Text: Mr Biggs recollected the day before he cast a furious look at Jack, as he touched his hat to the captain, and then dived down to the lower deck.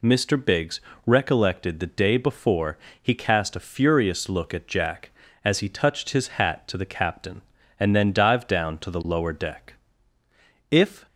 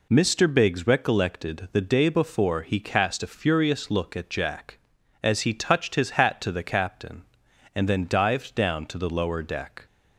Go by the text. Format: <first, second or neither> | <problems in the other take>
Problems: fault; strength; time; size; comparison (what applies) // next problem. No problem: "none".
second | pauses between "Biggs" and "recollected"; slight; at 0.8 s; 0.24 s long // pauses between "before" and "he"; slight; at 2.7 s; 0.22 s long // goes on to say "If"; slight; from 10.7 s on; 0.34 s long